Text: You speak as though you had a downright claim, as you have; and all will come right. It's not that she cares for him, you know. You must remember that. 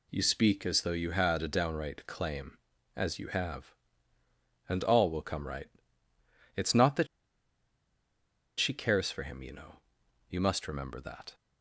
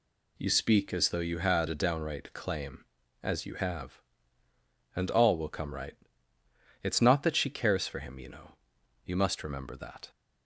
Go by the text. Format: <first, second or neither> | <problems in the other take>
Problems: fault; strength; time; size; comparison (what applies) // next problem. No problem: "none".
second | pauses between "that" and "she"; strong; at 7.0 s; 1.5 s long